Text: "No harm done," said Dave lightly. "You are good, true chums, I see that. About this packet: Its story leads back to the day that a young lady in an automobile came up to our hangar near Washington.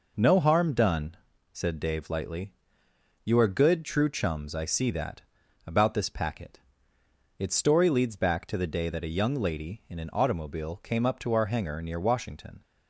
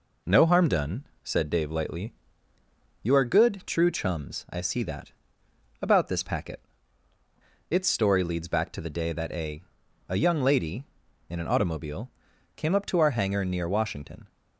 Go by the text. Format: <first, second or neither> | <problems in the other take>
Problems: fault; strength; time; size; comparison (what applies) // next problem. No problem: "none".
first | says "a" twice; at 10.0 s // pauses between "automobile" and "came"; at 12.1 s; 0.44 s long